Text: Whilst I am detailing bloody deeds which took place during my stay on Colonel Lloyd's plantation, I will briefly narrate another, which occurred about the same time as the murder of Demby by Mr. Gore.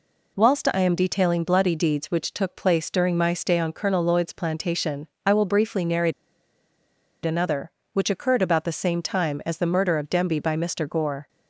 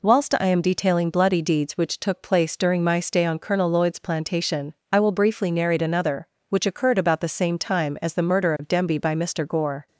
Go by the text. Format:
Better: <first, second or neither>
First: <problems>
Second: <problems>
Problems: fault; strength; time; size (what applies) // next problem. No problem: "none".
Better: second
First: pauses between "narrate" and "another"; at 6.1 s; 1.1 s long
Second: none